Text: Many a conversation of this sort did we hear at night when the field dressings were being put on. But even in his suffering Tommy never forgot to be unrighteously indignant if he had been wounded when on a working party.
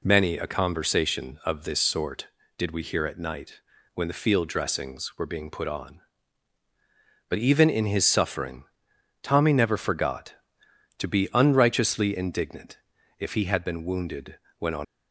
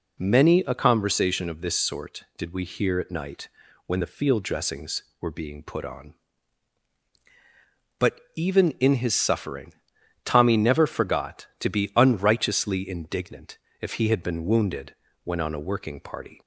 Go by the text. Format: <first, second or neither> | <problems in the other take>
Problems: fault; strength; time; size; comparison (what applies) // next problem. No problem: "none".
second | pauses between "night" and "when"; slight; at 3.6 s; 0.34 s long; also in the second // pauses between "suffering" and "Tommy"; noticeable; at 8.6 s; 0.56 s long; noticeable in the second // pauses between "indignant" and "if"; at 12.7 s; 0.40 s long; slight in the second // pauses between "wounded" and "when"; slight; at 14.3 s; 0.20 s long; slight in the second // stops before "a working party"; at 14.8 s